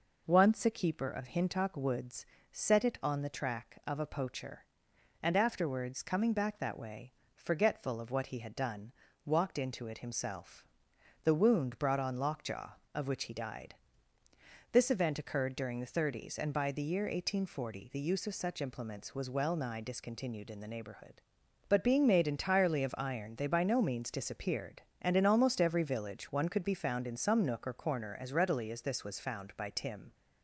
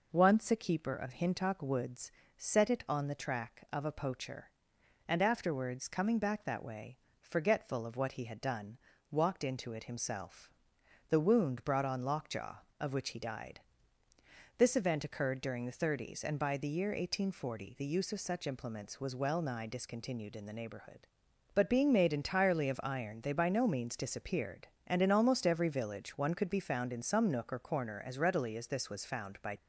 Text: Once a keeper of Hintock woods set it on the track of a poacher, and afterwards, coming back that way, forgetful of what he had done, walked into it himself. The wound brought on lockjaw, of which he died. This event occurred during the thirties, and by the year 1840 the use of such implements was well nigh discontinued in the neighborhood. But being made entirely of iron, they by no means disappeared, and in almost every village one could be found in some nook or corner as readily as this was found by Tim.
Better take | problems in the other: first | pauses between "woods" and "set"; slight; at 2.0 s; 0.26 s long; slight in the first // stops before "Tim"; at 29.5 s

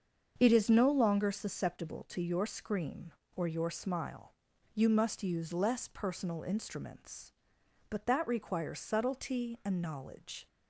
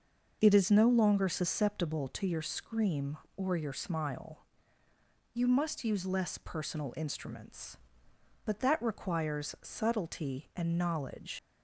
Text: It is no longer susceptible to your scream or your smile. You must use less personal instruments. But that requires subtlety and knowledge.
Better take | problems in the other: first | starts louder than the rest; noticeable; until 1.4 s; 6 dB; also in the first // leaves "knowledge" unfinished; at 11.3 s; 85 ms

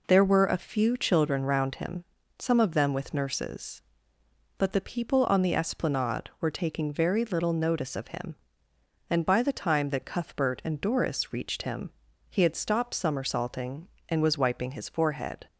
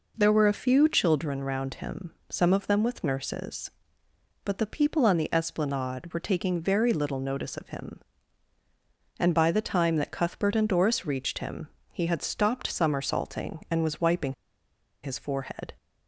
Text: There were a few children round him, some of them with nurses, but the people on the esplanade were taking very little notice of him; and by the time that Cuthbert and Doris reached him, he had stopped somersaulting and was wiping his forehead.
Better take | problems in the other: first | pauses between "wiping" and "his"; noticeable; at 14.3 s; 0.69 s long

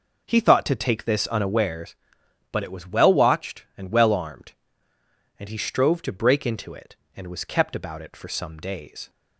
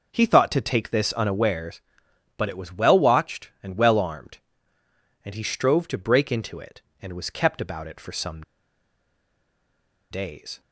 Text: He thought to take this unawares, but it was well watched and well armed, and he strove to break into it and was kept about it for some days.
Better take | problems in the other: first | pauses between "some" and "days"; strong; at 8.4 s; 1.6 s long

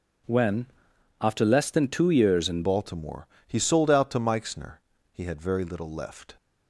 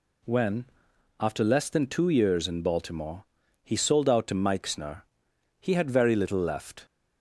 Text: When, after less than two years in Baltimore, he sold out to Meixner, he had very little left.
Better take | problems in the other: second | changes voice at "Baltimore"; from 2.6 s on; 3.7 s long

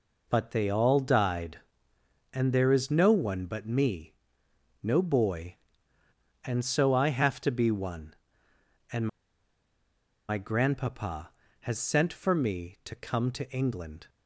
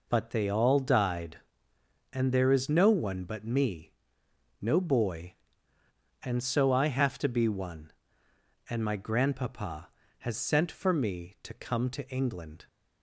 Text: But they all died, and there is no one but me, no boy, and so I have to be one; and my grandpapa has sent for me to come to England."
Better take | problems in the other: second | pauses between "and" and "my"; at 9.0 s; 1.2 s long

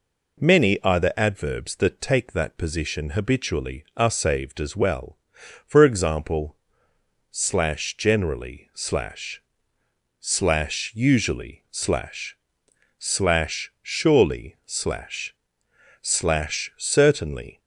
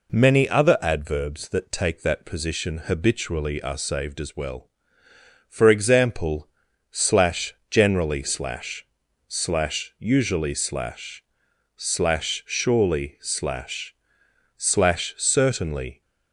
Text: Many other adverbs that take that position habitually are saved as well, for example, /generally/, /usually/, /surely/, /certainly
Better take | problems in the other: second | says "either" for "other"; at 0.8 s

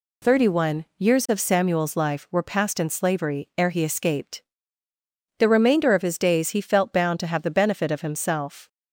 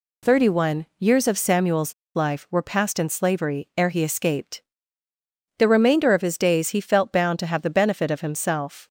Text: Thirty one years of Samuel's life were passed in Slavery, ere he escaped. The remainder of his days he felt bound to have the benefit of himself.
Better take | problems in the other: first | pauses between "Samuel's" and "life"; slight; at 1.9 s; 0.22 s long

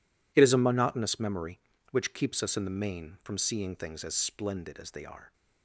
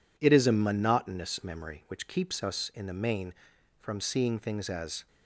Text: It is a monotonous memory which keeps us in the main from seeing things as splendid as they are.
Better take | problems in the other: first | stops before "splendid as they are"; at 5.0 s

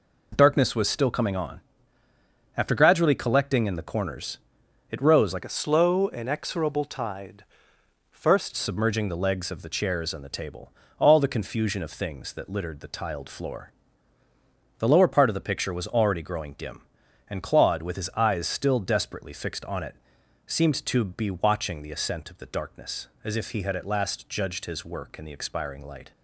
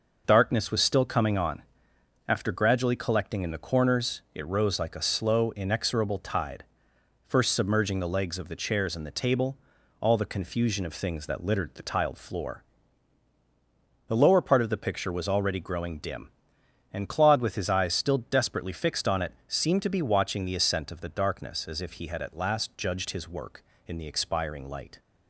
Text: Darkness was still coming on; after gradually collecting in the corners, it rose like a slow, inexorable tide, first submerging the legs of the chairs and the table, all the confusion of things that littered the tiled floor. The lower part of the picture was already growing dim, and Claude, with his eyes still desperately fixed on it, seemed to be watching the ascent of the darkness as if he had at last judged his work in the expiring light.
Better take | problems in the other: second | changes voice from "a" to "first"; from 5.4 to 8.5 s; 3.1 s long

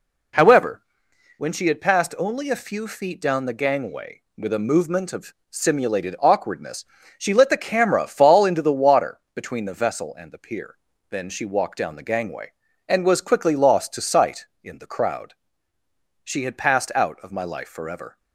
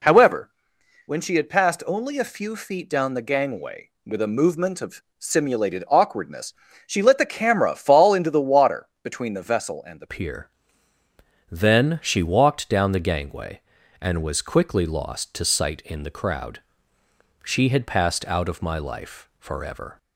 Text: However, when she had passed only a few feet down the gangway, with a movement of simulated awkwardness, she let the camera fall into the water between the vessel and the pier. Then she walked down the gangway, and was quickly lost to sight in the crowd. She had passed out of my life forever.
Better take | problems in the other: first | pauses between "of" and "simulated"; slight; at 5.0 s; 0.18 s long; slight in the first // pauses between "water" and "between"; slight; at 8.8 s; 0.16 s long; slight in the first // changes voice at "pier"; from 10.0 s on; 9.9 s long

